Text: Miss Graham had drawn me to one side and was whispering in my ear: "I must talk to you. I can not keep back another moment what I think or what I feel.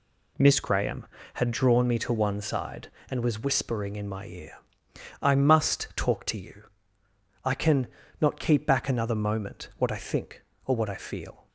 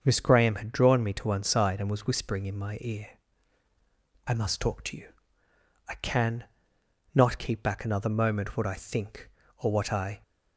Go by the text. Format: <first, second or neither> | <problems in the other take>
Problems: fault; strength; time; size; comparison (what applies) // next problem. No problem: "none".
first | starts louder than the rest; until 1.0 s; 6.5 dB // pauses between "can" and "not"; noticeable; at 6.4 s; 0.68 s long; slight in the first // stops before "feel"; at 10.2 s